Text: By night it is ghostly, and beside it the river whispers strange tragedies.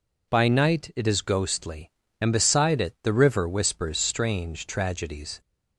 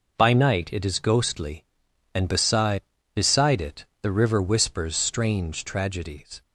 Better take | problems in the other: first | says "beside" twice; at 3.1 s // pauses between "it" and "the"; slight; at 3.8 s; 0.18 s long

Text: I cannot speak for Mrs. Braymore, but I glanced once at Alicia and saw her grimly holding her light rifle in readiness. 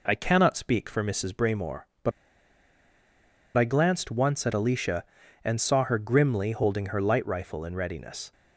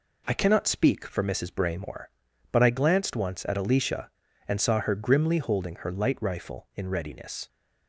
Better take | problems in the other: second | pauses between "but" and "I"; strong; at 2.1 s; 1.4 s long

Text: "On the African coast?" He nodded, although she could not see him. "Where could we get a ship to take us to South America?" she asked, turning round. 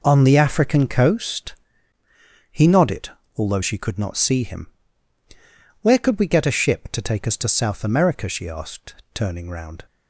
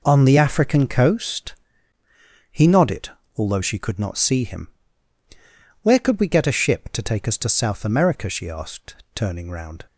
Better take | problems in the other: neither | none

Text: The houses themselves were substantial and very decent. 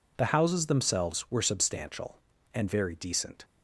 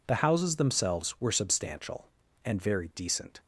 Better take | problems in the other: neither | none

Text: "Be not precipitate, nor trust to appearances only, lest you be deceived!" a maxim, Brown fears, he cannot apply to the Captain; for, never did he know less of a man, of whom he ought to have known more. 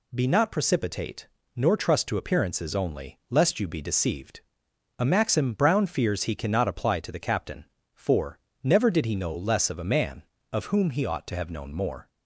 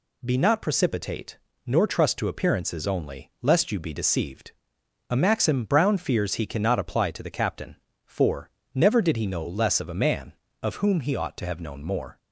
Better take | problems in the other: neither | none

